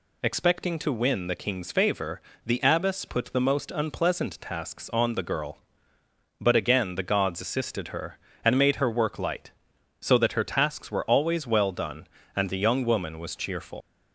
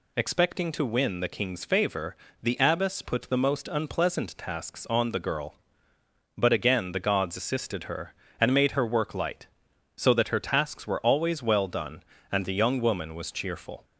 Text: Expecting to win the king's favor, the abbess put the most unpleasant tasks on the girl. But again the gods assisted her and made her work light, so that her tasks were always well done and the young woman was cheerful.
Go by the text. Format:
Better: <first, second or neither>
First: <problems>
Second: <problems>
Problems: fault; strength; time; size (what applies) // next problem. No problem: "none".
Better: second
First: leaves "cheerful" unfinished; at 13.8 s; 80 ms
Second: none